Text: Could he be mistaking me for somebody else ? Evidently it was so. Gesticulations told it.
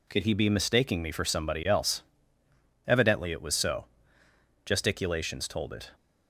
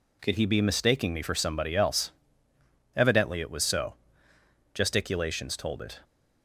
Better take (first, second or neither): neither